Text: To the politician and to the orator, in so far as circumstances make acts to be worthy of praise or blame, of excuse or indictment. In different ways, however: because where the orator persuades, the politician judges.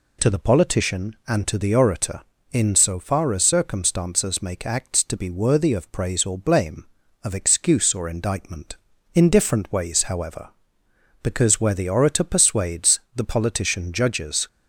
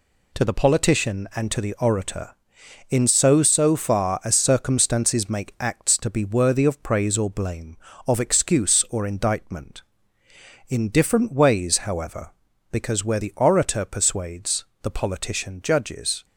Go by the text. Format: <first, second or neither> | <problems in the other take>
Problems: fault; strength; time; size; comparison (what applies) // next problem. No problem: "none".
first | says "so" twice; at 3.4 s